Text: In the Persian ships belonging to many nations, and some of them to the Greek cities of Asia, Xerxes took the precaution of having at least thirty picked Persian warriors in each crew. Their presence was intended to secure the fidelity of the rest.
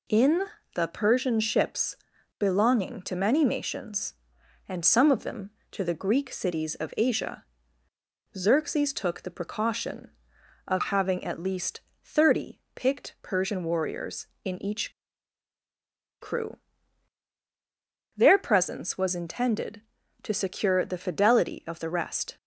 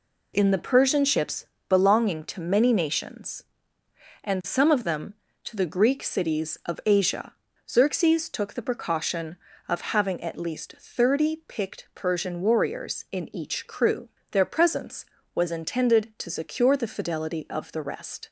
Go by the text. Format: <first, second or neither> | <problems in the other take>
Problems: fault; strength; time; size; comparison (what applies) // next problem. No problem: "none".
second | pauses between "In" and "the"; slight; at 0.4 s; 0.30 s long // pauses between "ships" and "belonging"; at 1.9 s; 0.44 s long; slight in the second // pauses between "least" and "thirty"; slight; at 11.8 s; 0.20 s long // pauses between "each" and "crew"; strong; at 14.9 s; 1.2 s long